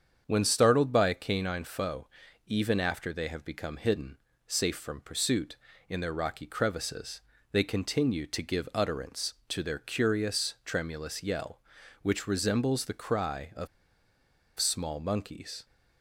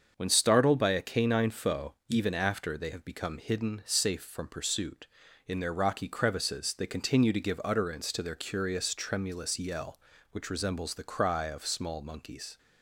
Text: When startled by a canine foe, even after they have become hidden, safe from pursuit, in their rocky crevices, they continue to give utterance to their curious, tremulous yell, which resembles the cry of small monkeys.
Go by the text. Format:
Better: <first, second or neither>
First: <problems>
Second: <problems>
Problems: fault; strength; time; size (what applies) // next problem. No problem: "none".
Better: second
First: starts louder than the rest; strong; until 1.2 s; 7.5 dB // pauses between "of" and "small"; noticeable; at 13.6 s; 0.91 s long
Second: starts louder than the rest; until 1.1 s; 7 dB